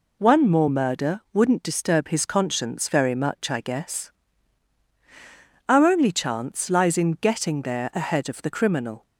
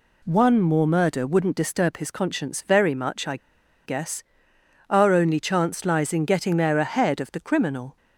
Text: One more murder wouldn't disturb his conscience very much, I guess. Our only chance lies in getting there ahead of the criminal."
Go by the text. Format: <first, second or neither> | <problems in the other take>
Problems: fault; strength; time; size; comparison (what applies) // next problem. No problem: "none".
first | pauses between "I" and "guess"; noticeable; at 3.3 s; 0.49 s long